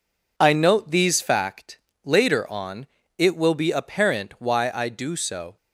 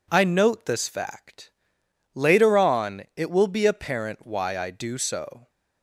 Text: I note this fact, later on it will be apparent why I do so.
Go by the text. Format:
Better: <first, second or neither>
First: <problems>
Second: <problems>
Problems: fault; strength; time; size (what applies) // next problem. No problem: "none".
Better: second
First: says "these" for "this"; at 0.9 s // pauses between "on" and "it"; slight; at 2.8 s; 0.30 s long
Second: none